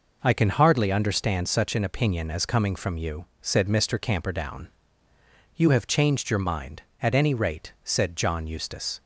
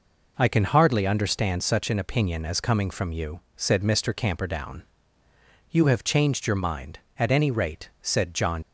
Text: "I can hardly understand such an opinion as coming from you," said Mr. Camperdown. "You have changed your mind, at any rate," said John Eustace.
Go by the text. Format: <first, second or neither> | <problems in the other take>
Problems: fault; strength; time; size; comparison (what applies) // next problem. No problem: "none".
first | stops before "Eustace"; at 8.6 s